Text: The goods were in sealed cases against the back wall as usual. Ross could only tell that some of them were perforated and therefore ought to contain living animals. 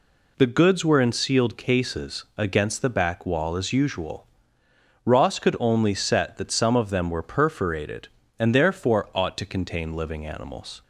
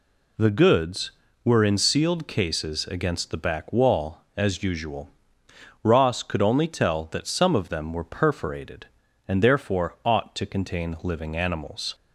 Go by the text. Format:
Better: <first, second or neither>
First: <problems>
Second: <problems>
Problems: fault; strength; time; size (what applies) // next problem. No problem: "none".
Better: second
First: says "set" for "tell"; at 5.9 s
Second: none